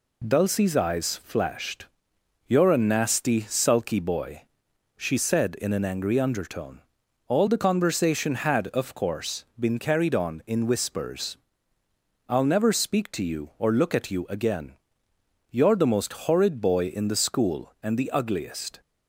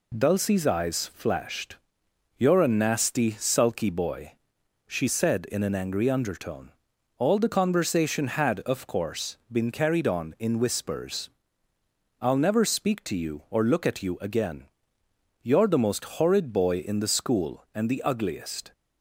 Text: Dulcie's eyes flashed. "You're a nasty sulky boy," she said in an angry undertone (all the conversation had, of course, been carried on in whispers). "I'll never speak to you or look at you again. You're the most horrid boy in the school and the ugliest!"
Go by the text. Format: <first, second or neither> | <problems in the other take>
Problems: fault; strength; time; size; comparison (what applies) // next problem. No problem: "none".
neither | pauses between "most" and "horrid"; slight; the same in both